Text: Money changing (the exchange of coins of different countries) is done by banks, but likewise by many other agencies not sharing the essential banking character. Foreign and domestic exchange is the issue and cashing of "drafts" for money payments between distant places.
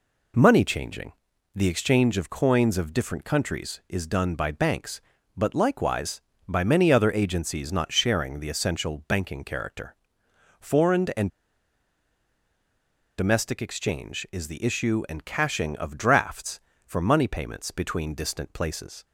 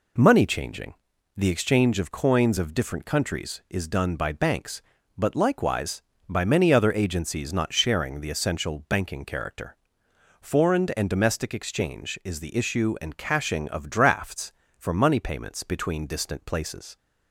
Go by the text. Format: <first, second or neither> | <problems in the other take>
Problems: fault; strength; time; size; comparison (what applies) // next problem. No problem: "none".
second | pauses between "and" and "domestic"; strong; at 11.2 s; 1.8 s long